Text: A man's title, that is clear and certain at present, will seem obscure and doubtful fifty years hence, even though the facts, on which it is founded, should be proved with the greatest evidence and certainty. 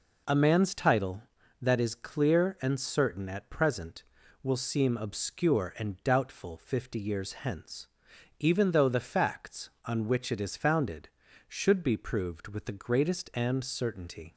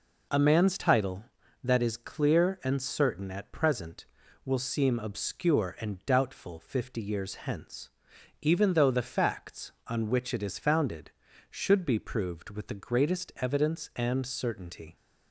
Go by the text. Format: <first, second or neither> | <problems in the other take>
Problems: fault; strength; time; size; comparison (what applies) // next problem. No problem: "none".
second | skips "evidence"; at 13.3 s